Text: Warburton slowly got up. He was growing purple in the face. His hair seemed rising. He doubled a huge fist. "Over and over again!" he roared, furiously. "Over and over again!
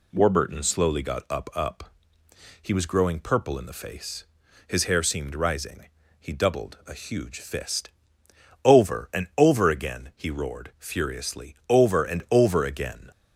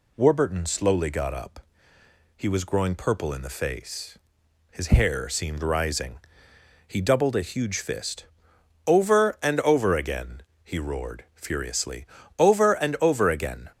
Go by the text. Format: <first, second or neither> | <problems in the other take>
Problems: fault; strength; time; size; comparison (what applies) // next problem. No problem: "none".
second | says "up" twice; at 1.5 s